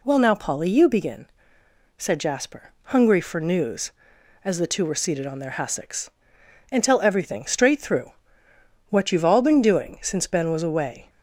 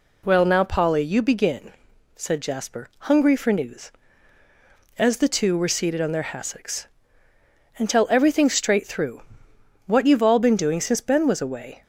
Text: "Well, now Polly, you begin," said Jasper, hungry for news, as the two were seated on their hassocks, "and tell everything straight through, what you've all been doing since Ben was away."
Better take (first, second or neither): neither